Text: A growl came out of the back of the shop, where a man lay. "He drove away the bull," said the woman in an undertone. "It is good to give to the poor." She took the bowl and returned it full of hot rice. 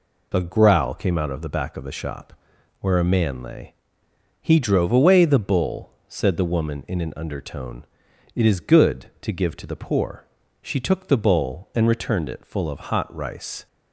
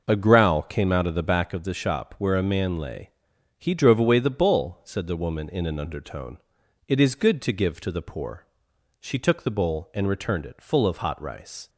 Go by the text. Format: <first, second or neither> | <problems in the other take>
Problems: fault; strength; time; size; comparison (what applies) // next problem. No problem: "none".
first | starts louder than the rest; noticeable; until 1.7 s; 6 dB